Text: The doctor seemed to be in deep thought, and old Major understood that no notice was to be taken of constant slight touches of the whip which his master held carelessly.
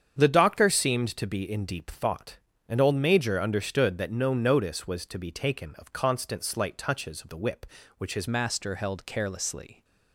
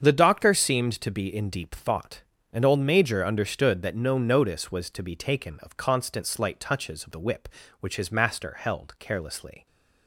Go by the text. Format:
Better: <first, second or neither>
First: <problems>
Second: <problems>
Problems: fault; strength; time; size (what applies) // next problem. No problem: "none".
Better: second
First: starts louder than the rest; strong; until 1.2 s; 8 dB // changes voice at "master"; from 8.2 s on; 1.6 s long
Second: starts louder than the rest; strong; until 1.0 s; 7.5 dB